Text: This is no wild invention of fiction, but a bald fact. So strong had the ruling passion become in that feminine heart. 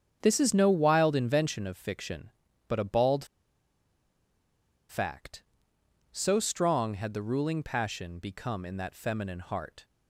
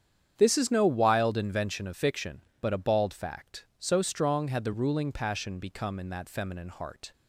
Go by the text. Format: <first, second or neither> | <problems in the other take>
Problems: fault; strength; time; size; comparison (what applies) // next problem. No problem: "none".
second | starts louder than the rest; strong; until 1.2 s; 8 dB; strong in the second // pauses between "bald" and "fact"; strong; at 3.2 s; 1.6 s long